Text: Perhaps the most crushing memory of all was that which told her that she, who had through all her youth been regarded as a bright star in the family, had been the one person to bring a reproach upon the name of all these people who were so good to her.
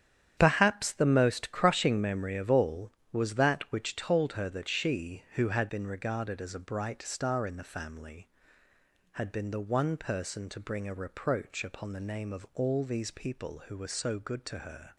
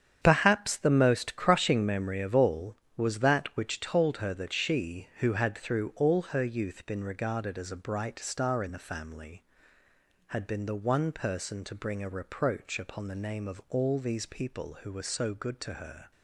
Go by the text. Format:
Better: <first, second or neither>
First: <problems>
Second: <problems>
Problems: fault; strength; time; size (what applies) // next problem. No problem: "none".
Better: second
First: starts louder than the rest; strong; until 1.3 s; 9.5 dB // skips "through all her youth"; at 5.6 s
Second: starts louder than the rest; strong; until 1.2 s; 8.5 dB